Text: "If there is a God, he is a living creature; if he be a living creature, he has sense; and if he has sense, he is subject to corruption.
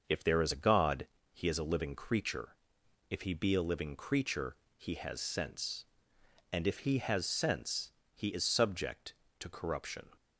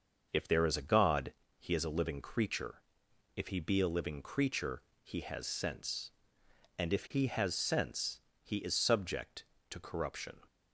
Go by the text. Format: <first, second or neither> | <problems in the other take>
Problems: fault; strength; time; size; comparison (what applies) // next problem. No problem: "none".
neither | starts louder than the rest; the same in both